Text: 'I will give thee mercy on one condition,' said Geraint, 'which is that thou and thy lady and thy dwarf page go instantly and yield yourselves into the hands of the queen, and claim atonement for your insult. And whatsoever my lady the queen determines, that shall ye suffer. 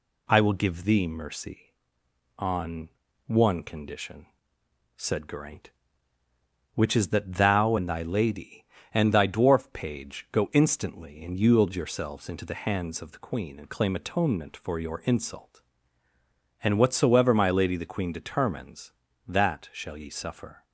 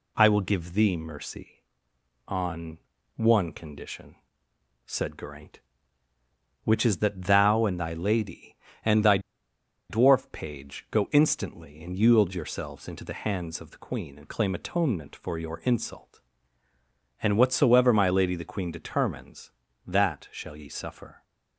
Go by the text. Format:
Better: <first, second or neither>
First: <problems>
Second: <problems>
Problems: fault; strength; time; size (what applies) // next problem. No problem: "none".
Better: first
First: pauses between "on" and "one"; at 2.8 s; 0.38 s long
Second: pauses between "on" and "one"; at 2.7 s; 0.38 s long // pauses between "thy" and "dwarf"; noticeable; at 9.1 s; 0.70 s long